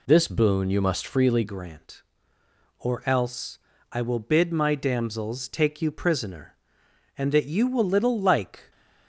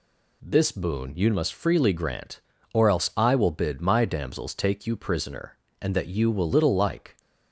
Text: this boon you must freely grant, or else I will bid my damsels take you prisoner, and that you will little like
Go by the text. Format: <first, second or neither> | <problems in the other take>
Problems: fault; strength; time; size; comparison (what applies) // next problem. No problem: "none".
second | changes voice at "grant"; from 1.4 s on; 7.3 s long // pauses between "else" and "I"; slight; at 3.5 s; 0.34 s long